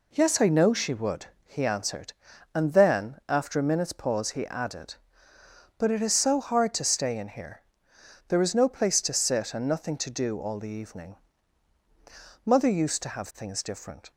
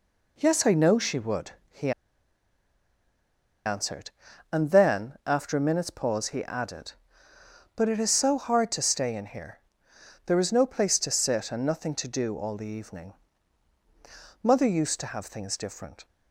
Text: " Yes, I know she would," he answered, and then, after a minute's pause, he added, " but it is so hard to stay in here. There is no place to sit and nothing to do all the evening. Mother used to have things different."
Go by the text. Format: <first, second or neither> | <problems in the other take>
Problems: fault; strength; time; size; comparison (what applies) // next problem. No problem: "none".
first | pauses between "he" and "answered"; strong; at 1.9 s; 1.7 s long